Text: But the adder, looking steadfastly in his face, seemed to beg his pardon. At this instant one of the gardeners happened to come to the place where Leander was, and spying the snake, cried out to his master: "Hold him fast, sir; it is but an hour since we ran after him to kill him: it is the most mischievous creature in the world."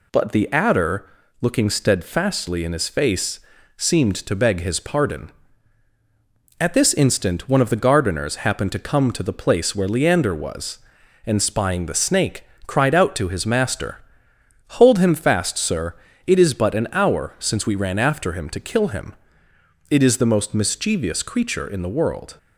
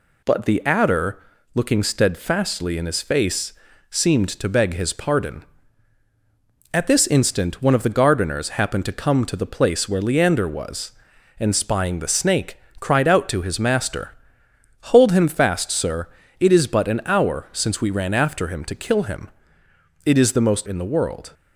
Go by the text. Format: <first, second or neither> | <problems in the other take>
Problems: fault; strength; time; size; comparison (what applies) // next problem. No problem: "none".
first | skips "mischievous creature"; at 20.6 s